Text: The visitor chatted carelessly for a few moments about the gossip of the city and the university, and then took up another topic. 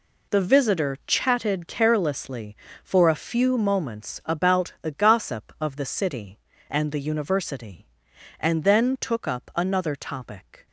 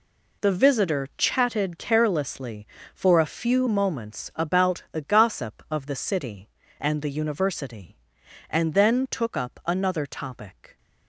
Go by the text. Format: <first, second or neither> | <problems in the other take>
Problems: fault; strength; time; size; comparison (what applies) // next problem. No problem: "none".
neither | none